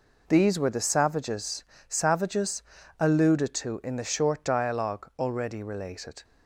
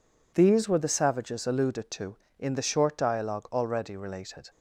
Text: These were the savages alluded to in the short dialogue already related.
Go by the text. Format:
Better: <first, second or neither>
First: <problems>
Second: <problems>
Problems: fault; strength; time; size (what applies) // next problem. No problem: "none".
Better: second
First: says "savages" twice; at 1.8 s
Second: none